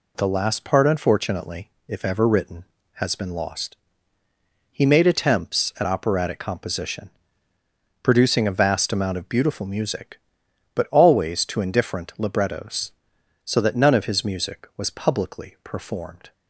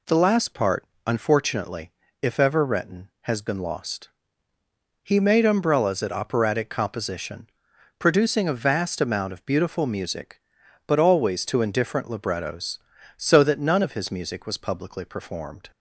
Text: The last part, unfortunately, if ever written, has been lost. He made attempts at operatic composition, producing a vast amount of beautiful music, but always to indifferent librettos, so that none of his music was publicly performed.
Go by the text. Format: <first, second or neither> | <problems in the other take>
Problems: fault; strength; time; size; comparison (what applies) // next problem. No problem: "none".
first | says "umbrellas" for "attempts"; at 5.4 s